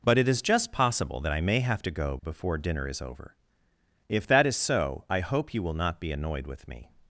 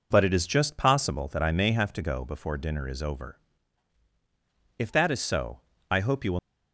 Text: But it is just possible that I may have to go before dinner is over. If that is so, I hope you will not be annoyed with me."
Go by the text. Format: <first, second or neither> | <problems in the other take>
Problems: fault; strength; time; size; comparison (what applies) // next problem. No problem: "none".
first | stops before "not be annoyed with me"; at 6.3 s